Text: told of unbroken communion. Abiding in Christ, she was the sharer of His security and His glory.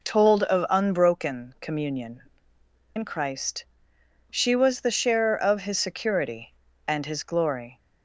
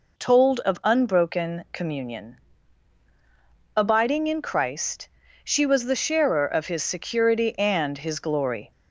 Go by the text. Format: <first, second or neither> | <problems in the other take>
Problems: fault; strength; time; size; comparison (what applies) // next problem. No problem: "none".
second | skips "Abiding"; at 2.5 s